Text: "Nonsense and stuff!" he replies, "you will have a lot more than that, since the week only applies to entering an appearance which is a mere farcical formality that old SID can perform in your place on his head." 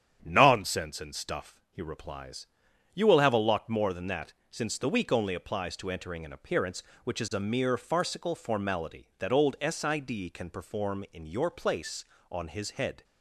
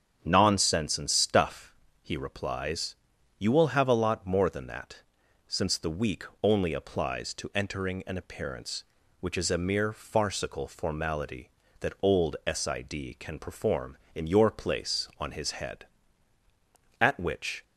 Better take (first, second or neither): first